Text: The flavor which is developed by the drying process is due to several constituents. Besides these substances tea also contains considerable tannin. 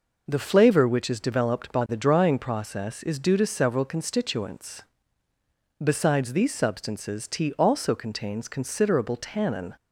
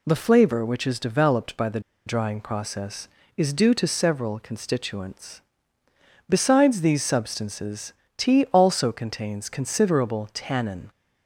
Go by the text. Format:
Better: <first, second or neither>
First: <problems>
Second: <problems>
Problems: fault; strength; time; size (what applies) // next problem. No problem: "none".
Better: first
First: none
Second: pauses between "the" and "drying"; slight; at 1.7 s; 0.26 s long // pauses between "substances" and "tea"; slight; at 7.9 s; 0.26 s long